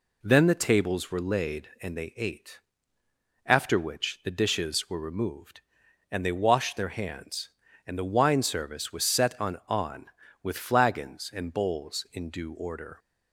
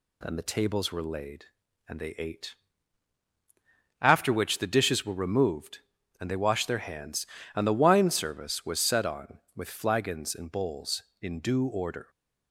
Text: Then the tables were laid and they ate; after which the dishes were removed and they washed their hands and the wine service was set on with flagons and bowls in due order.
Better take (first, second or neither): second